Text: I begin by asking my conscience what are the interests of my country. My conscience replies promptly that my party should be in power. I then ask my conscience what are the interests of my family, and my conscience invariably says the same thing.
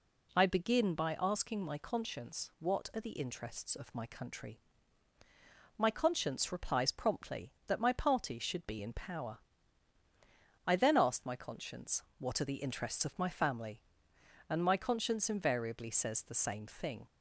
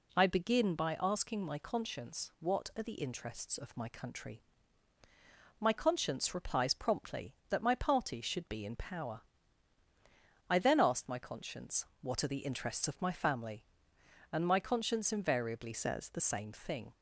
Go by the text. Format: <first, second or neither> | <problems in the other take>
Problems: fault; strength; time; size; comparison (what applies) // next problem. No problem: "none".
first | pauses between "conscience" and "what"; slight; at 11.8 s; 0.16 s long; slight in the first // changes voice from "says" to "the"; from 15.7 to 16.2 s; 0.5 s long